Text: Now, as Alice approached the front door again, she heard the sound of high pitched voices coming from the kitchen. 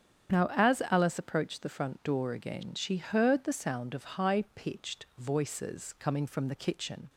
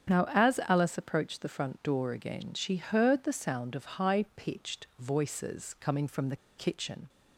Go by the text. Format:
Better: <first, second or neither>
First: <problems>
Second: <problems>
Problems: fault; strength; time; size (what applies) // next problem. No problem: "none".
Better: first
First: starts louder than the rest; strong; until 1.4 s; 8.5 dB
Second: starts louder than the rest; strong; until 1.2 s; 8.5 dB // pauses between "the" and "kitchen"; slight; at 6.3 s; 0.20 s long